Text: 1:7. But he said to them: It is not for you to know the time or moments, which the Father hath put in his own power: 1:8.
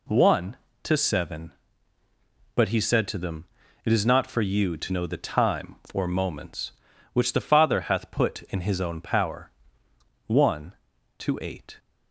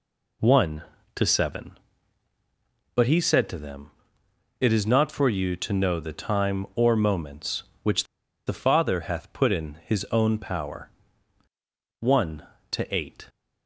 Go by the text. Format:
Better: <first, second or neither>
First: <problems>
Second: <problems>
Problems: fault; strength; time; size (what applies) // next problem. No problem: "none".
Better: first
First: none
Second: pauses between "which" and "the"; at 8.0 s; 0.42 s long